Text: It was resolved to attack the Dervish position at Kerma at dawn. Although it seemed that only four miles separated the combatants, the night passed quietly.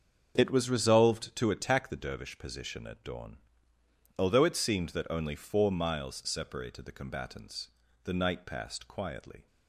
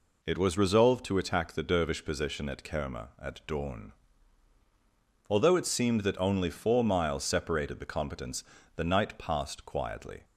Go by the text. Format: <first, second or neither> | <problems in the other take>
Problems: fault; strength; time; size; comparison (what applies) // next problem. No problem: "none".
second | starts louder than the rest; until 1.3 s; 7 dB // skips "at Kerma"; at 2.8 s